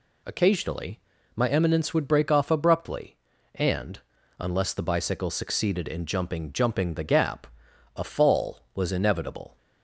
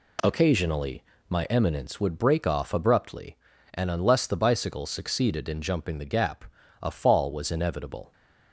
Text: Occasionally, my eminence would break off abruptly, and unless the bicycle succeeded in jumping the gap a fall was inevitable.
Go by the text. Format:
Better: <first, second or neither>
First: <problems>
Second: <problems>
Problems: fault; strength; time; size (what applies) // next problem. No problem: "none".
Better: second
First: pauses between "and" and "unless"; at 3.9 s; 0.40 s long // says "jumping" twice; at 6.5 s // pauses between "gap" and "a"; noticeable; at 7.4 s; 0.48 s long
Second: pauses between "gap" and "a"; at 6.4 s; 0.38 s long